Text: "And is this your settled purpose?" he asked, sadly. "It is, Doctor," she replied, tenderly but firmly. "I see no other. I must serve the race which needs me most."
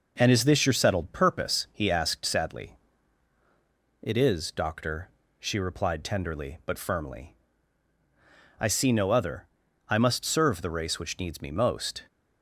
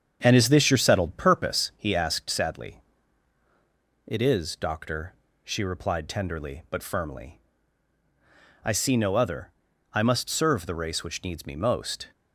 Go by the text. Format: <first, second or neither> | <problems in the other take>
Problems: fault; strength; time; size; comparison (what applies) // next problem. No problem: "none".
first | starts louder than the rest; strong; until 1.8 s; 7.5 dB